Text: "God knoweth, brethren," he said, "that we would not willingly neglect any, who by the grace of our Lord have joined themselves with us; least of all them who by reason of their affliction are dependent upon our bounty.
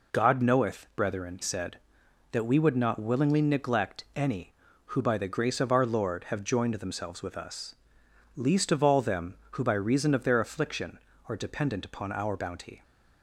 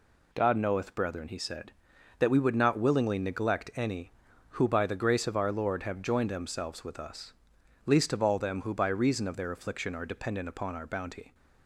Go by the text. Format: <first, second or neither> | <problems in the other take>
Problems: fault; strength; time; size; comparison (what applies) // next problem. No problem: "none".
second | skips "he"; at 1.4 s